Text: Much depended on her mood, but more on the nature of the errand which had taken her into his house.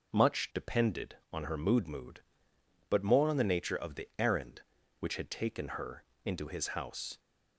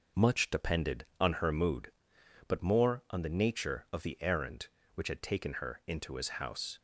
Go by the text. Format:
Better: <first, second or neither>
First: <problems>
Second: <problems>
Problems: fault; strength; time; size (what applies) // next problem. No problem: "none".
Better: second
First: says "mood" twice; at 1.8 s // pauses between "her" and "into"; slight; at 6.0 s; 0.22 s long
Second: none